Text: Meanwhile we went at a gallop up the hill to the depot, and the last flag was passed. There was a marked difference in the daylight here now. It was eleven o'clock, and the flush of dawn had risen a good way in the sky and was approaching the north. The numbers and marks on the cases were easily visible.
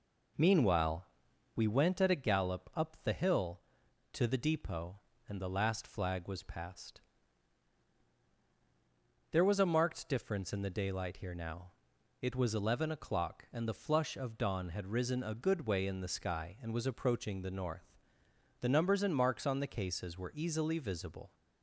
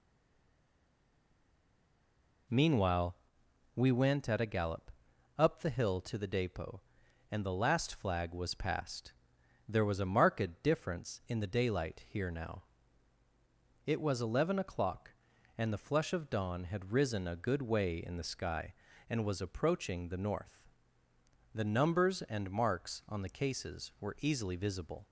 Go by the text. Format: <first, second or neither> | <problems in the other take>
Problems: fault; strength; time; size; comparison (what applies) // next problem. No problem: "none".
first | stays silent before the first word; until 2.4 s; 2.4 s long // pauses between "Meanwhile" and "we"; noticeable; at 3.1 s; 0.60 s long; noticeable in the first // pauses between "gallop" and "up"; noticeable; at 4.8 s; 0.48 s long